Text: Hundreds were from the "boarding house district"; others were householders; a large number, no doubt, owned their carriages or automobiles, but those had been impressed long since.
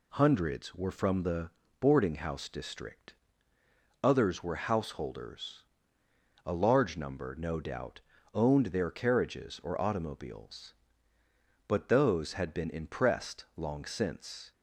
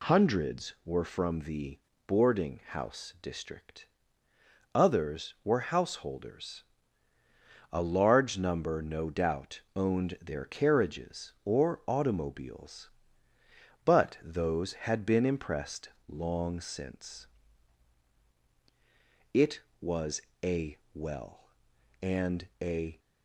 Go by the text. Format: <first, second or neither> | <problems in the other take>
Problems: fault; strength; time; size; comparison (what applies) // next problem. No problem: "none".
first | pauses between "the" and "boarding"; slight; at 1.7 s; 0.28 s long; slight in the first // pauses between "impressed" and "long"; slight; at 15.8 s; 0.18 s long // goes on to say "It was a well and a"; strong; from 19.3 s on; 3.6 s long